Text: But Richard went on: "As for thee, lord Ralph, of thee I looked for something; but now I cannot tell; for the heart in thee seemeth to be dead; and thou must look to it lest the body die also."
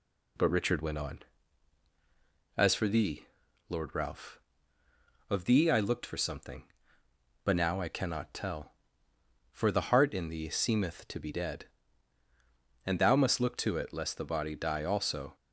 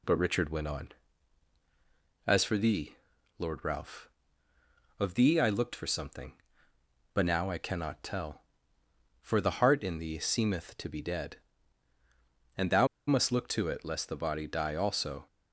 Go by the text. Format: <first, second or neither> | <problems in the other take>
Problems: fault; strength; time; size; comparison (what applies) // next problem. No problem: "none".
first | pauses between "thou" and "must"; slight; at 12.8 s; 0.21 s long